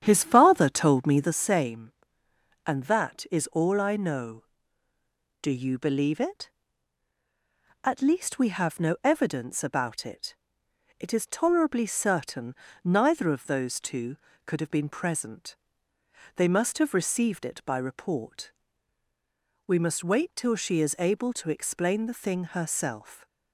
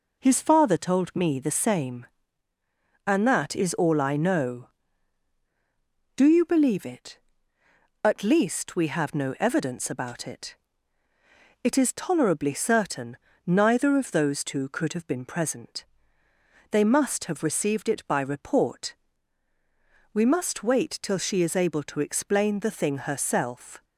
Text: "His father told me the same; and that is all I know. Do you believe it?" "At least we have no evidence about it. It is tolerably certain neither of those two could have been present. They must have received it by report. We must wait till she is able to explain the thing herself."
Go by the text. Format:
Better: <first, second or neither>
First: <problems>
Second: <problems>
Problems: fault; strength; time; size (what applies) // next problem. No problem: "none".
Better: second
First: starts louder than the rest; strong; until 1.4 s; 9.5 dB // pauses between "certain" and "neither"; slight; at 12.5 s; 0.30 s long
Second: pauses between "certain" and "neither"; slight; at 13.1 s; 0.30 s long